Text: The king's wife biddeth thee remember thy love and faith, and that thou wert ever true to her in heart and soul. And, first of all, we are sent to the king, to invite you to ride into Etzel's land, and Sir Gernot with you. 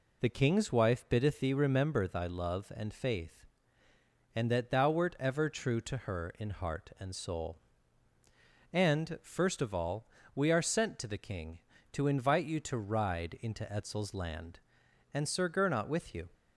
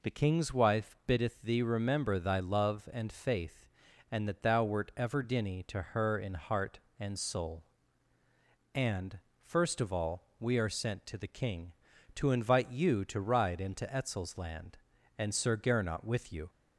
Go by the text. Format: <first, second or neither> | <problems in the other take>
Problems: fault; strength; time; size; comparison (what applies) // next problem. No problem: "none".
first | says "dinny" for "true"; at 5.2 s